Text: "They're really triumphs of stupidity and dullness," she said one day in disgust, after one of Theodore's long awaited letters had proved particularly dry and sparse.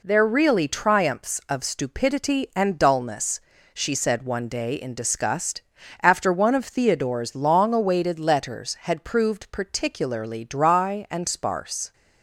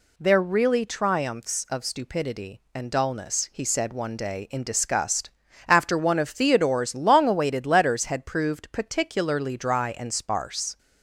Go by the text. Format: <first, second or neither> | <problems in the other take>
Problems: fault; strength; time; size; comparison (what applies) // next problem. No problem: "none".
first | says "he" for "she"; at 3.5 s